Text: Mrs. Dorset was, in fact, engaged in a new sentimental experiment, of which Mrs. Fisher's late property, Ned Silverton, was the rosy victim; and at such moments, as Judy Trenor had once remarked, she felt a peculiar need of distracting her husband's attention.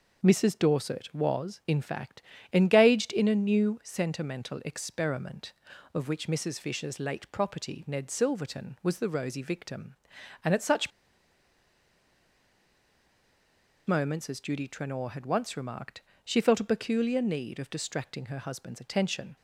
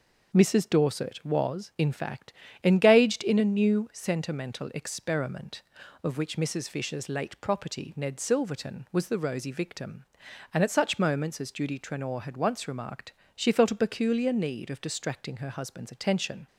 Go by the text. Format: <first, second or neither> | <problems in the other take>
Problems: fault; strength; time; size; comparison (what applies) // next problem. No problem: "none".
second | pauses between "such" and "moments"; strong; at 10.9 s; 2.9 s long